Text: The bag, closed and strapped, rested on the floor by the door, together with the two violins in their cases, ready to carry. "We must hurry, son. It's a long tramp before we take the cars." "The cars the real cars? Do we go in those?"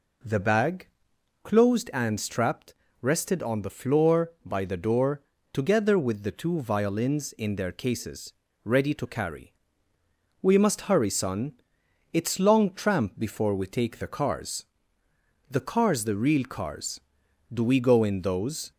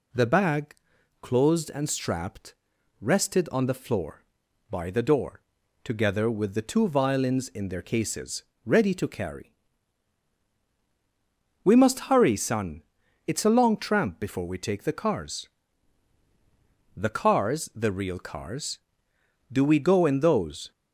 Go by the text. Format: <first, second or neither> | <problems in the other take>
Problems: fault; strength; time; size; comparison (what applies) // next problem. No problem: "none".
second | skips "a"; at 12.3 s